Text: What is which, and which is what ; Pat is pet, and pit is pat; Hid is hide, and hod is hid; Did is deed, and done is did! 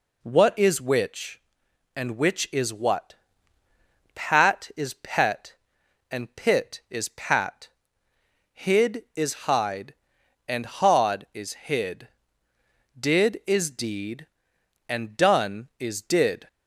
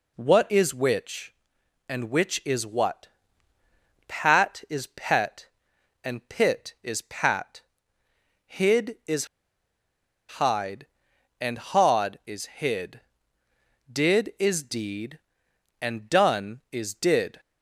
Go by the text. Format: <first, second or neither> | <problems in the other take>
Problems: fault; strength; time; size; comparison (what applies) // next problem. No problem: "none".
first | pauses between "is" and "hide"; at 9.2 s; 1.1 s long